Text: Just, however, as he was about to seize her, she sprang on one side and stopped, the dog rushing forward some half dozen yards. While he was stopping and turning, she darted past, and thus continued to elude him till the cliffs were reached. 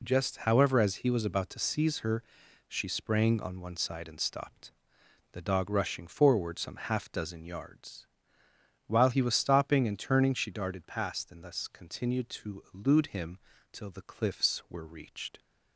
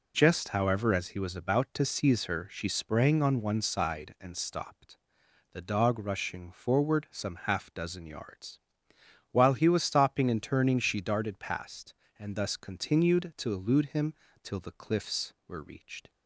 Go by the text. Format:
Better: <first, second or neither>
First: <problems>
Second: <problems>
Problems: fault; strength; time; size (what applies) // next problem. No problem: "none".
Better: neither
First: pauses between "him" and "till"; slight; at 13.3 s; 0.34 s long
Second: pauses between "him" and "till"; slight; at 14.1 s; 0.32 s long